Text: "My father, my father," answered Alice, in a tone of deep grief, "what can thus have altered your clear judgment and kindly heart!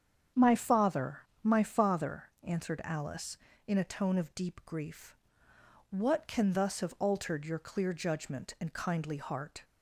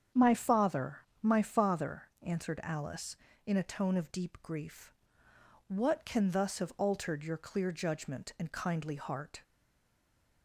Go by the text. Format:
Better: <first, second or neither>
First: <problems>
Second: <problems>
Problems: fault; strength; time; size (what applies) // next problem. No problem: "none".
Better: first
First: starts louder than the rest; strong; until 1.5 s; 8 dB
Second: starts louder than the rest; strong; until 1.3 s; 8 dB // stays silent after the last word; from 9.4 s on; 1.0 s long